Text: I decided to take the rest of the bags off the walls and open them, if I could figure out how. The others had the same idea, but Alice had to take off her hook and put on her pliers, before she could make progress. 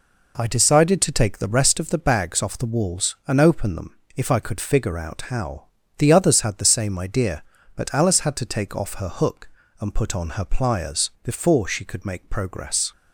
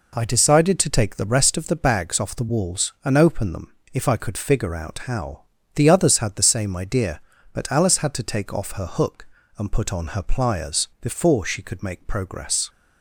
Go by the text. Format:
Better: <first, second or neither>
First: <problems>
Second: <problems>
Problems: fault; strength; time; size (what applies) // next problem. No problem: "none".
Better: neither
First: none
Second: none